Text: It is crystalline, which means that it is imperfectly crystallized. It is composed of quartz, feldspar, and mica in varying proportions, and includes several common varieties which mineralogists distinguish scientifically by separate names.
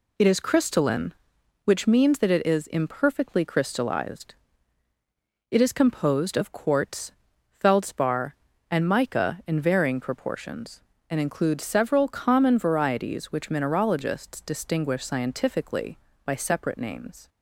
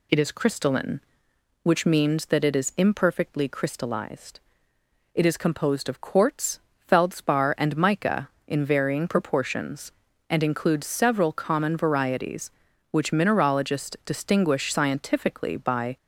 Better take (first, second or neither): first